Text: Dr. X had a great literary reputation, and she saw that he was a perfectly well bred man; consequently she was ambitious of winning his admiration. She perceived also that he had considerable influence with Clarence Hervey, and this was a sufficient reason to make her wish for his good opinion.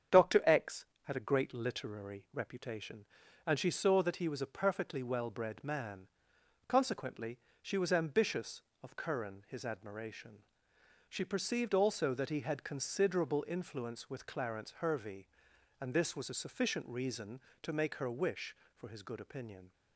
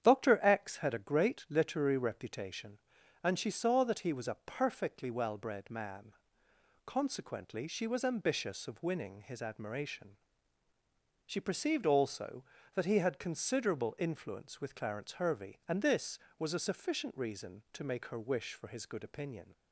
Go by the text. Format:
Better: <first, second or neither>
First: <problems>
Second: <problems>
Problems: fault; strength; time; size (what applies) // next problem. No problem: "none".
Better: second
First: starts louder than the rest; strong; until 1.3 s; 8 dB // pauses between "consequently" and "she"; slight; at 7.3 s; 0.20 s long // says "curran" for "winning"; at 8.9 s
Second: starts louder than the rest; strong; until 1.0 s; 9 dB